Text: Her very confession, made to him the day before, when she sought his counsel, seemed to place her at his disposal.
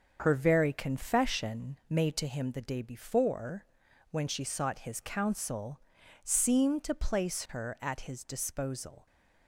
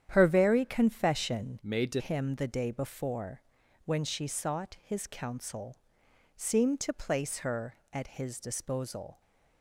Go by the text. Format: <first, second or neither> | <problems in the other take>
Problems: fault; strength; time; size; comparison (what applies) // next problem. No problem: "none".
first | starts louder than the rest; strong; until 1.1 s; 9.5 dB; also in the first // changes voice from "made" to "to"; from 1.6 to 2.0 s; 0.4 s long